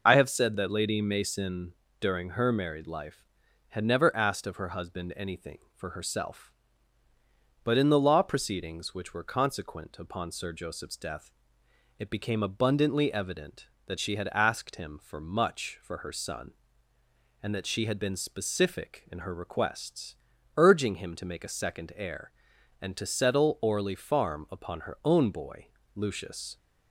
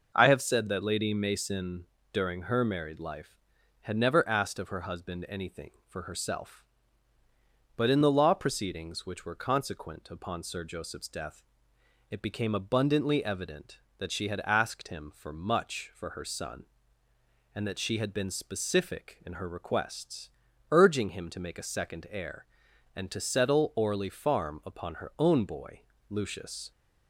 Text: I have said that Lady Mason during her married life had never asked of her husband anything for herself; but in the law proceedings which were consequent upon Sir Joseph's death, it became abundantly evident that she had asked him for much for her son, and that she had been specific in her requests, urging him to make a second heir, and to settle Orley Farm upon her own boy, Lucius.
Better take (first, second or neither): second